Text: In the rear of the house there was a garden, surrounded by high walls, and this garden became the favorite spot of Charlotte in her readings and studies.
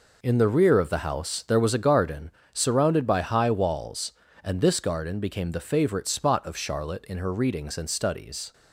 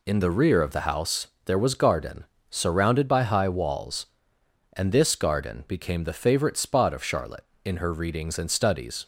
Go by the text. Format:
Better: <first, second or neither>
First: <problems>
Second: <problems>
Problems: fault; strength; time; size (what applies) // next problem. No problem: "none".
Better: first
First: none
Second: pauses between "house" and "there"; slight; at 1.2 s; 0.18 s long // skips "a"; at 1.7 s